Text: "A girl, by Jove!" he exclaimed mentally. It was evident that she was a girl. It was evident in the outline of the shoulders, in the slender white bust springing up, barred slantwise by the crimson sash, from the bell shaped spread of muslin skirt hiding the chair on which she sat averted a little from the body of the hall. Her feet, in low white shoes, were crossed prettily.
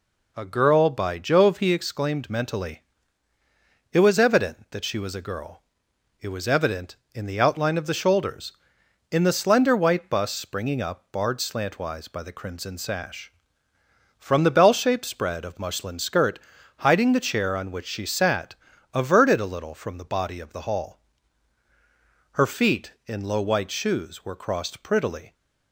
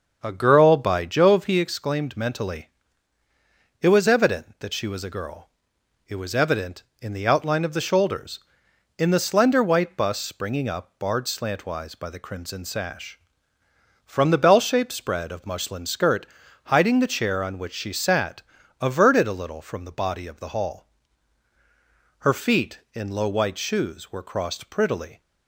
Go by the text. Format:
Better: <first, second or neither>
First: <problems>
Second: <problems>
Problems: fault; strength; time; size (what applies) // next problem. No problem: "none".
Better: first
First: pauses between "skirt" and "hiding"; at 16.3 s; 0.40 s long // pauses between "sat" and "averted"; at 18.5 s; 0.40 s long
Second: starts louder than the rest; until 1.3 s; 6.5 dB // pauses between "skirt" and "hiding"; at 16.2 s; 0.40 s long // pauses between "sat" and "averted"; at 18.4 s; 0.40 s long